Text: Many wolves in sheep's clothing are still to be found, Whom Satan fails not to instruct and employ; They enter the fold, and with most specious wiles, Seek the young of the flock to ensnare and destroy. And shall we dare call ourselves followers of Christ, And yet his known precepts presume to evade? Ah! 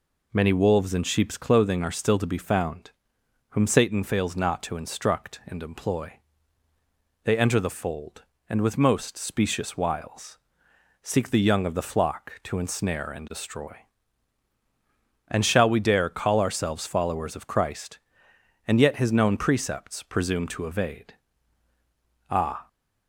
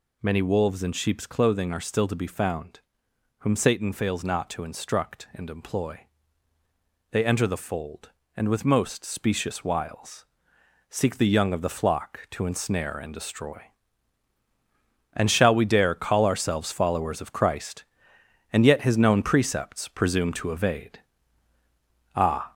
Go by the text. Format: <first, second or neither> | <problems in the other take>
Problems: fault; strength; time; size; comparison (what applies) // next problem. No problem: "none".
first | gets louder; noticeable; throughout; 5 dB